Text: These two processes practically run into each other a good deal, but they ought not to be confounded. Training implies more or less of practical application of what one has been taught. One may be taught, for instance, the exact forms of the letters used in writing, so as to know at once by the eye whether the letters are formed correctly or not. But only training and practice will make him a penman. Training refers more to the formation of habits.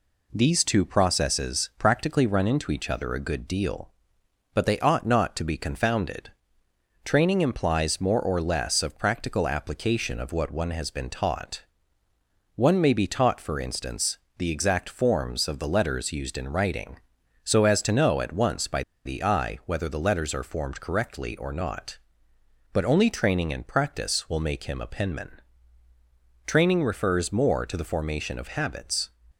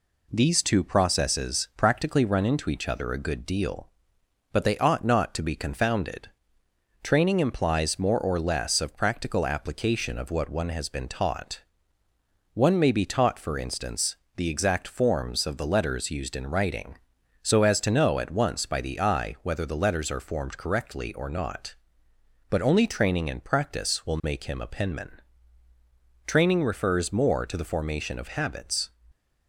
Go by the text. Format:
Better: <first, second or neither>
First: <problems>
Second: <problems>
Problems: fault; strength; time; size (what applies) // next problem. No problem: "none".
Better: second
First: pauses between "by" and "the"; slight; at 18.8 s; 0.22 s long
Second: none